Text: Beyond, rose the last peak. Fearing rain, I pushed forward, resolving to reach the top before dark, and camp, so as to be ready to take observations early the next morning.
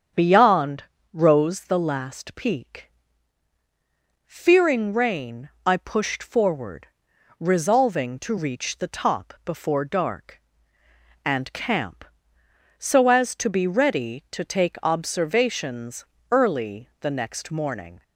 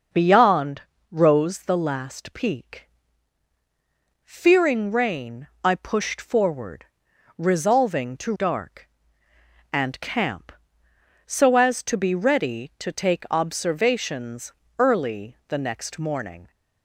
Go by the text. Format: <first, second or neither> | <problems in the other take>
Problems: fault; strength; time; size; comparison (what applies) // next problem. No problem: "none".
first | starts louder than the rest; until 1.4 s; 6 dB; strong in the first // skips "reach the top before"; at 8.3 s // pauses between "observations" and "early"; slight; at 14.5 s; 0.26 s long; slight in the first